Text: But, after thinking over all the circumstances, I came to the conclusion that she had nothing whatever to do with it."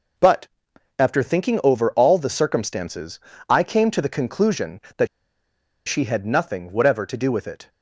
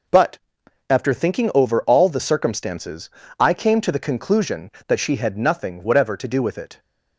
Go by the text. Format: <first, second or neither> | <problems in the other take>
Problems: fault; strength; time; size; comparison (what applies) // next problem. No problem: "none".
second | pauses between "that" and "she"; noticeable; at 5.0 s; 0.81 s long